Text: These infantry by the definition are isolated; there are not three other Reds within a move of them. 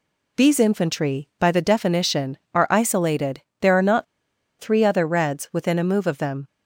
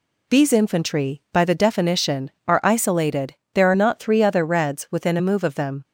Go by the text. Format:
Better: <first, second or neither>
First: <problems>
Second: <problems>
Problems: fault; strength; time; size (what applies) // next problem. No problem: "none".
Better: second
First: pauses between "not" and "three"; noticeable; at 4.0 s; 0.55 s long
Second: none